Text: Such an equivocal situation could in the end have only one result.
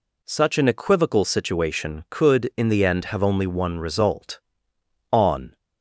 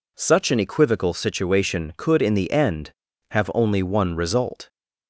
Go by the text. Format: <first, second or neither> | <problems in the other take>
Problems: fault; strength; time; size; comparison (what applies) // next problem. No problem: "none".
second | goes on to say "On"; slight; from 5.1 s on; 0.46 s long